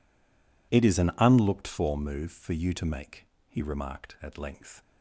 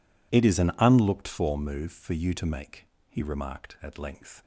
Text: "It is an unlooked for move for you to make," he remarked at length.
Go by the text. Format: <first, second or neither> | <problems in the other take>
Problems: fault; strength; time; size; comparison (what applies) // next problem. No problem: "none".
second | stays silent before the first word; slight; until 0.7 s; 0.7 s long